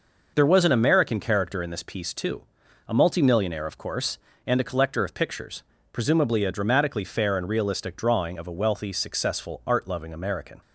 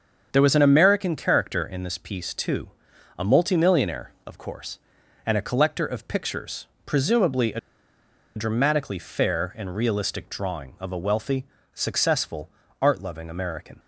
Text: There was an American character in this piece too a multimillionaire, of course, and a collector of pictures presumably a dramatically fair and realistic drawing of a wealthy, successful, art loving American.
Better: first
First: pauses between "too" and "a"; at 2.4 s; 0.42 s long // pauses between "pictures" and "presumably"; slight; at 5.6 s; 0.28 s long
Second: starts louder than the rest; until 1.3 s; 7 dB // pauses between "too" and "a"; noticeable; at 2.6 s; 0.50 s long // pauses between "pictures" and "presumably"; slight; at 6.6 s; 0.18 s long // pauses between "a" and "dramatically"; noticeable; at 7.5 s; 0.77 s long

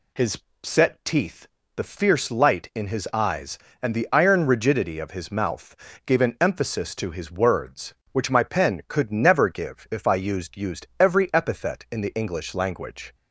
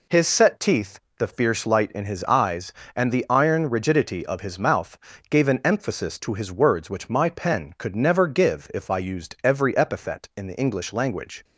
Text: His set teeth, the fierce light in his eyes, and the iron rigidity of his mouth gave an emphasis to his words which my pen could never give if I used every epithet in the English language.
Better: second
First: pauses between "His" and "set"; slight; at 0.3 s; 0.26 s long // pauses between "mouth" and "gave"; slight; at 5.7 s; 0.30 s long // says "used" twice; at 10.5 s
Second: pauses between "mouth" and "gave"; slight; at 4.9 s; 0.30 s long

